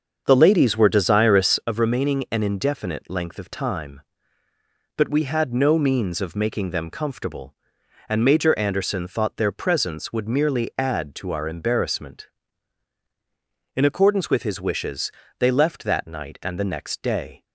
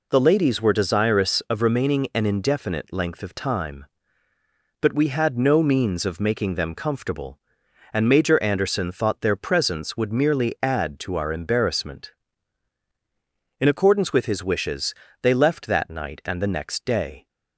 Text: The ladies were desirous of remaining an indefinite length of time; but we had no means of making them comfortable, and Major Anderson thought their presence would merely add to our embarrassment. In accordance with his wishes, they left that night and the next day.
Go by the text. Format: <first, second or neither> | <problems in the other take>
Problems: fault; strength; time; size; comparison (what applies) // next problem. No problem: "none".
second | starts louder than the rest; until 1.7 s; 6.5 dB